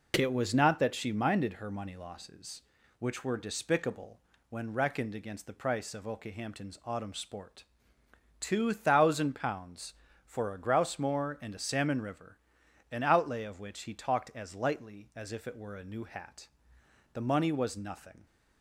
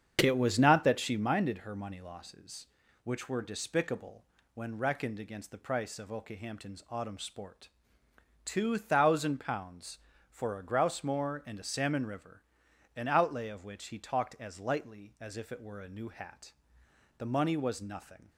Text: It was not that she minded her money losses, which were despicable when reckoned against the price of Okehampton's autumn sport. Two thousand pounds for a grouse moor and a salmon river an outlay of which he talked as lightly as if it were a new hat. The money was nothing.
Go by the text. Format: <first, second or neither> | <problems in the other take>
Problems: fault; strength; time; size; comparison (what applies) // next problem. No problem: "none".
first | starts louder than the rest; strong; until 1.3 s; 7.5 dB // pauses between "despicable" and "when"; slight; at 4.2 s; 0.28 s long; slight in the first // pauses between "river" and "an"; noticeable; at 12.4 s; 0.54 s long; noticeable in the first